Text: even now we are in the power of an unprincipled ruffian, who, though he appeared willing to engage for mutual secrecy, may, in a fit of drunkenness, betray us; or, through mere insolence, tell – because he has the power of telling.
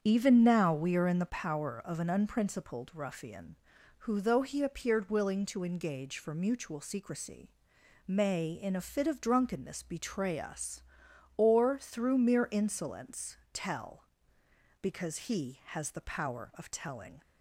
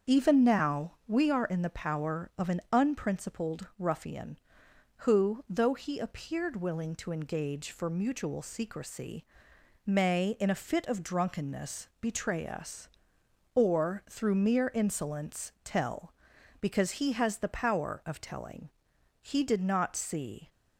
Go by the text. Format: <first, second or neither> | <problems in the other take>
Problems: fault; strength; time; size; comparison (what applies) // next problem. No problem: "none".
first | starts louder than the rest; strong; until 1.2 s; 7 dB; strong in the first // goes on to say "He did not see"; noticeable; from 19.2 s on; 1.2 s long